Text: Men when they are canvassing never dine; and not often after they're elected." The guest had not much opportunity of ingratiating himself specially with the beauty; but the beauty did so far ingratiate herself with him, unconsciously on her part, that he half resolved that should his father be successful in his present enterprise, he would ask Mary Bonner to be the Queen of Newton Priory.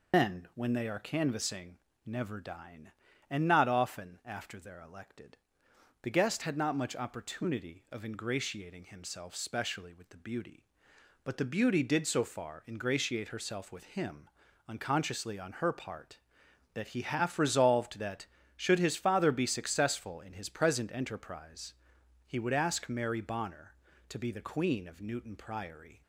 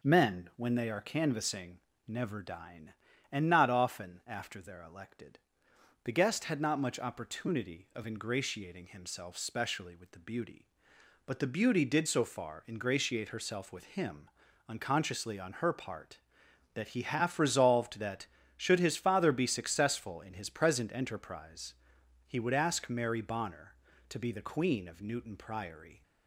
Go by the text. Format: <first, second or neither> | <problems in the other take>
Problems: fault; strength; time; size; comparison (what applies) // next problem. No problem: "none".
second | loses the start of "Men"; at 0.1 s; 120 ms // pauses between "canvassing" and "never"; slight; at 1.7 s; 0.28 s long; slight in the second